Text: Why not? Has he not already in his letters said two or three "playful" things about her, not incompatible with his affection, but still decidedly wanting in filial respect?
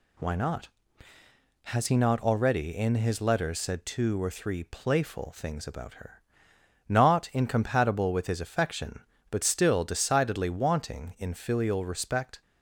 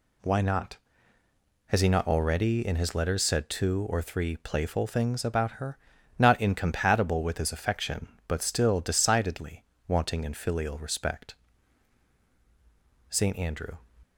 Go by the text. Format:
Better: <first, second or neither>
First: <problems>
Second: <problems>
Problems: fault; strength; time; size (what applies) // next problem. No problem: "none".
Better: first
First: none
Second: pauses between "decidedly" and "wanting"; slight; at 9.6 s; 0.24 s long // goes on to say "Saint Andrew"; noticeable; from 13.0 s on; 0.68 s long